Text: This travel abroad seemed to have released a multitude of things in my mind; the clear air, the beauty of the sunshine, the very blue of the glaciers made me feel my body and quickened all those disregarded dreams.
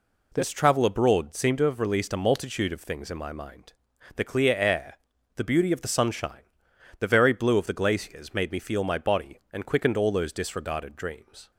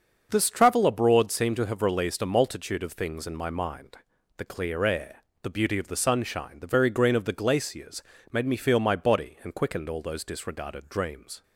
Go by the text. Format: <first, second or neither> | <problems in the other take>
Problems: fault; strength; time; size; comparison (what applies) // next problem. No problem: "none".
first | starts louder than the rest; until 1.3 s; 6.5 dB // says "green" for "blue"; at 6.8 s // pauses between "glaciers" and "made"; slight; at 8.0 s; 0.30 s long